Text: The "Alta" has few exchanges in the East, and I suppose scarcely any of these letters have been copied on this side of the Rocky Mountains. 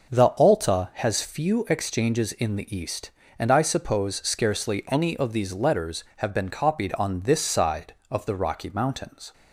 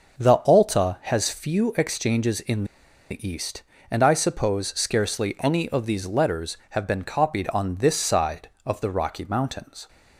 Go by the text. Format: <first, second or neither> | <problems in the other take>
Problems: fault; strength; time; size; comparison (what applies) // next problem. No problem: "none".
first | starts louder than the rest; noticeable; until 1.3 s; 6 dB // pauses between "in" and "the"; noticeable; at 2.6 s; 0.46 s long